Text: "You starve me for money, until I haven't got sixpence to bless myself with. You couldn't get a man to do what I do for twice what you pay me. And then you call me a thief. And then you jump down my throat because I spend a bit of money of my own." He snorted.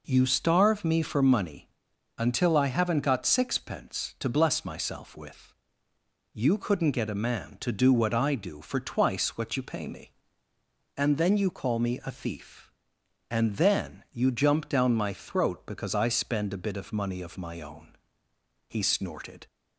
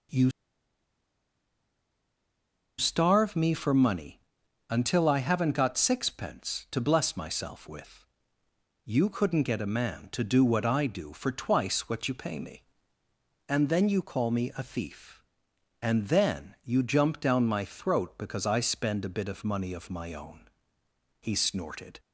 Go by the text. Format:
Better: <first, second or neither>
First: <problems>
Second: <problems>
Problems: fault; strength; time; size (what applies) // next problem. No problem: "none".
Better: first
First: none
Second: pauses between "You" and "starve"; strong; at 0.3 s; 2.4 s long